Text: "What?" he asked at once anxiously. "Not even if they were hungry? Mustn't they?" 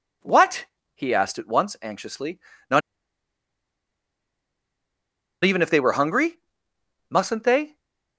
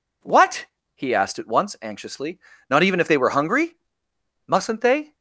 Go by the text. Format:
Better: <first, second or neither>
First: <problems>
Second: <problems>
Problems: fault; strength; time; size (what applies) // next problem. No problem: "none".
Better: second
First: pauses between "Not" and "even"; strong; at 2.8 s; 2.6 s long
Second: none